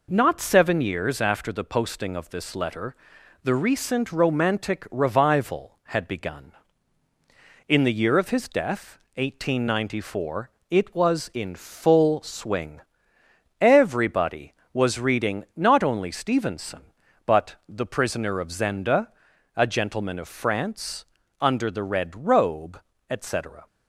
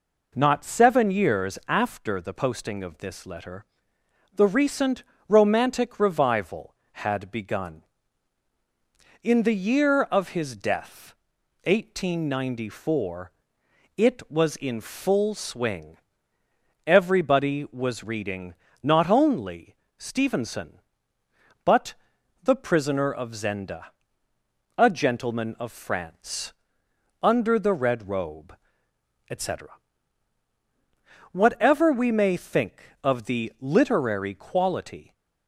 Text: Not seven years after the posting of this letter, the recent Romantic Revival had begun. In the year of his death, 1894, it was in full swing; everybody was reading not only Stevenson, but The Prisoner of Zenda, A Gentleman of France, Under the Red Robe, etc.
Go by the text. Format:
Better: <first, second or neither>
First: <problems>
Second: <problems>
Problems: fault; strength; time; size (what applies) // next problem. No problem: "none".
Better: first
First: none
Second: pauses between "recent" and "Romantic"; slight; at 5.0 s; 0.26 s long // pauses between "reading" and "not"; slight; at 18.5 s; 0.28 s long // pauses between "only" and "Stevenson"; slight; at 19.7 s; 0.22 s long // pauses between "but" and "The"; noticeable; at 21.9 s; 0.48 s long // goes on to say "Whatever we may think of the literary quality"; strong; from 31.3 s on; 3.8 s long